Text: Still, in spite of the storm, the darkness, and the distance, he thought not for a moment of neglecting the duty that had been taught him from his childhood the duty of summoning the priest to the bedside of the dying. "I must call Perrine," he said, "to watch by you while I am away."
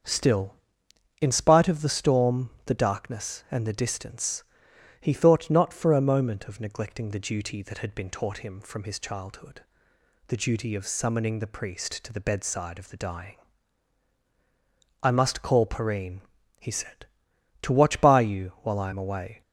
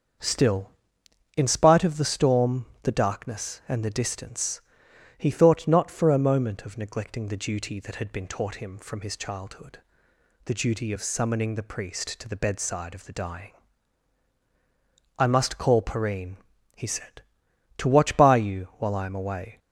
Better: neither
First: starts louder than the rest; until 1.7 s; 7 dB // pauses between "childhood" and "the"; noticeable; at 9.6 s; 0.68 s long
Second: starts louder than the rest; until 1.8 s; 7 dB // pauses between "childhood" and "the"; noticeable; at 9.7 s; 0.68 s long

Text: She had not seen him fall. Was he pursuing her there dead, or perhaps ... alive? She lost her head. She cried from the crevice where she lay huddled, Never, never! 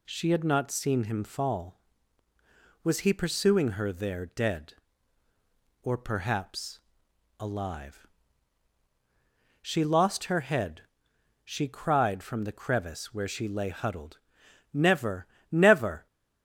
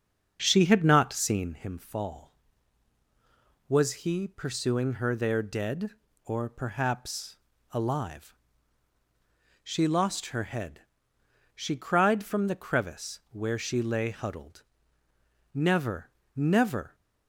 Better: first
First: none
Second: starts louder than the rest; until 1.5 s; 6.5 dB

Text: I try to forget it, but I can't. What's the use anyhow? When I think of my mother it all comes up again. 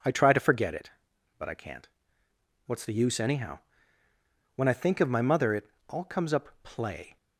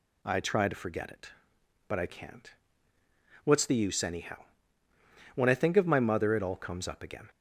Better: second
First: pauses between "it" and "all"; slight; at 5.6 s; 0.24 s long // says "play" for "again"; at 6.6 s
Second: none

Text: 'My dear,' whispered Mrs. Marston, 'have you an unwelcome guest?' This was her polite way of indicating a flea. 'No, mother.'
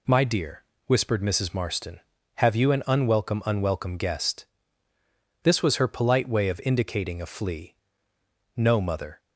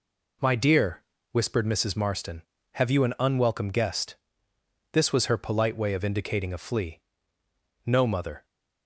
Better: second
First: says "unwelcome" twice; at 3.4 s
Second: none

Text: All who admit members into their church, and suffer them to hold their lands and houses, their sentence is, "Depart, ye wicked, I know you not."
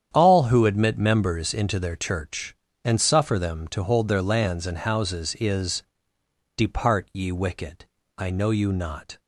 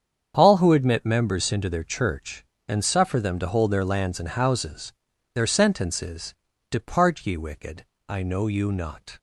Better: second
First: starts louder than the rest; strong; until 1.1 s; 9 dB // skips "their sentence"; at 5.3 s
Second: starts louder than the rest; strong; until 1.3 s; 8 dB

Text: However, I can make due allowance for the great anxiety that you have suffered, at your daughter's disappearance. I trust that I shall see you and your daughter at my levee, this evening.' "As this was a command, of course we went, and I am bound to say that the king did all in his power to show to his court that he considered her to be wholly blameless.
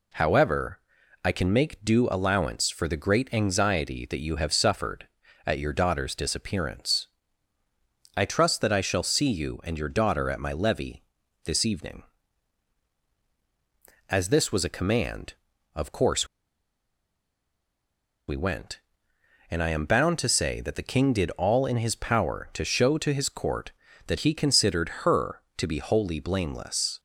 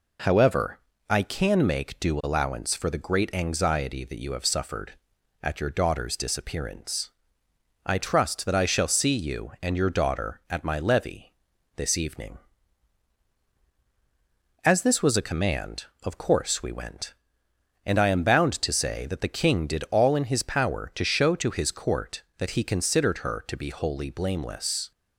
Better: second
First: pauses between "course" and "we"; strong; at 16.2 s; 2.0 s long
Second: none

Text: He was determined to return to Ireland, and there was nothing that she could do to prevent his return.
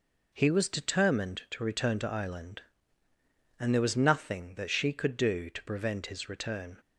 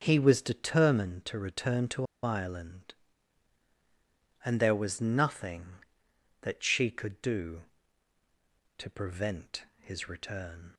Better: first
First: none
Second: starts louder than the rest; until 1.0 s; 7 dB // pauses between "to" and "Ireland"; slight; at 2.0 s; 0.18 s long

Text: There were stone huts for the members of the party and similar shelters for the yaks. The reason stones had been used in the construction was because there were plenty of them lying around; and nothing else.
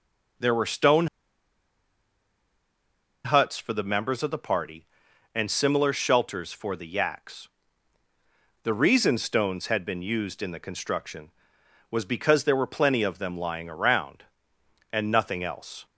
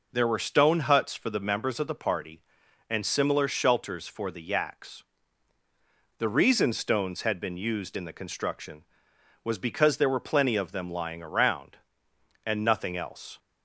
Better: second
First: pauses between "stone" and "huts"; strong; at 1.0 s; 2.1 s long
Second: none

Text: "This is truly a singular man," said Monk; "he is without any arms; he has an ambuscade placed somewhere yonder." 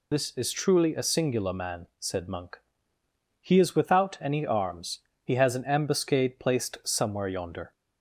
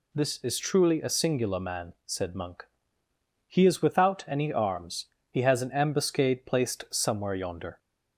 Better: second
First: loses the start of "This"; at 0.1 s; 40 ms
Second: none

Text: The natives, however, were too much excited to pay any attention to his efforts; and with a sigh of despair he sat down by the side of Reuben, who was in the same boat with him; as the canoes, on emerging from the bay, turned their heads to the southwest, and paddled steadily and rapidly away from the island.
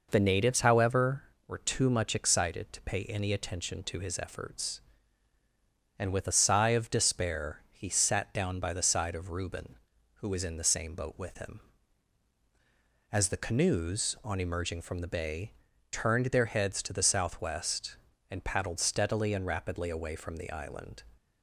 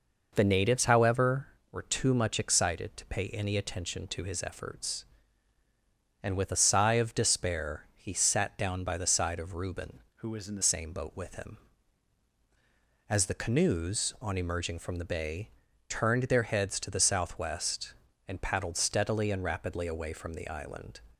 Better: first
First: none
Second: changes voice from "who" to "the"; from 10.1 to 10.6 s; 0.5 s long

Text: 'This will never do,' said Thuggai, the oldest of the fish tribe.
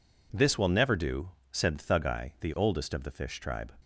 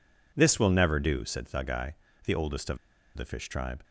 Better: first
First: none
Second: pauses between "of" and "the"; at 2.7 s; 0.38 s long

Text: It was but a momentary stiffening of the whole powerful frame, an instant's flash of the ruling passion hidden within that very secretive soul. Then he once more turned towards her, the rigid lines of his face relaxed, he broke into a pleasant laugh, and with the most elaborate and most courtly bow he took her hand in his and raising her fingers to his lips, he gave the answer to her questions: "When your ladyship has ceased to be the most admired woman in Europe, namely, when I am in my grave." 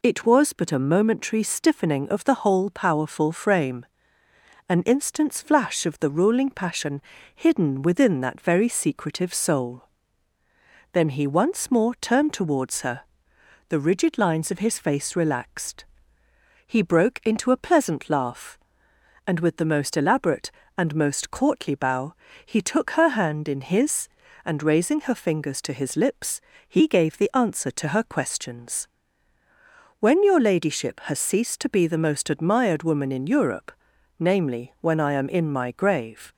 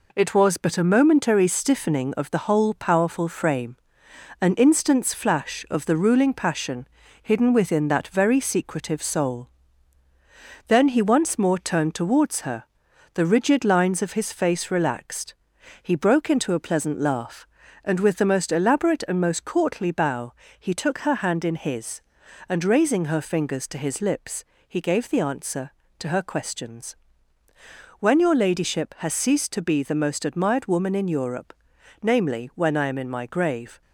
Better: first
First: pauses between "passion" and "hidden"; slight; at 7.0 s; 0.32 s long // pauses between "bow" and "he"; slight; at 22.1 s; 0.30 s long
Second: gets quieter; noticeable; throughout; 5 dB // pauses between "passion" and "hidden"; slight; at 6.8 s; 0.36 s long // pauses between "bow" and "he"; slight; at 20.3 s; 0.26 s long

